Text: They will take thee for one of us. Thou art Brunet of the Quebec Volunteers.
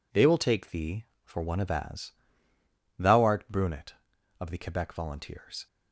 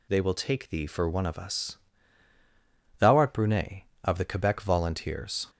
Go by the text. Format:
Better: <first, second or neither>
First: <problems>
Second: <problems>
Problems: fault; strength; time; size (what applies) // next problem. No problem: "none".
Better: second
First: says "as" for "us"; at 1.7 s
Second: none